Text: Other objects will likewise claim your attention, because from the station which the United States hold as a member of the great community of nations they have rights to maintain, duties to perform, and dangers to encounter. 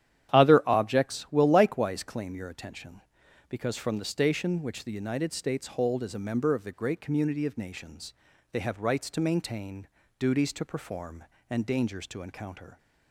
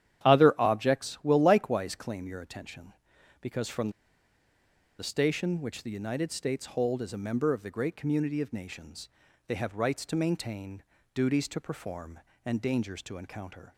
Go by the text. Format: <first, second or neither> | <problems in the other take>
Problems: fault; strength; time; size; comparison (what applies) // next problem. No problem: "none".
first | starts louder than the rest; strong; until 1.3 s; 11 dB; strong in the first // pauses between "from" and "the"; at 3.8 s; 1.0 s long // pauses between "nations" and "they"; at 9.0 s; 0.38 s long; also in the first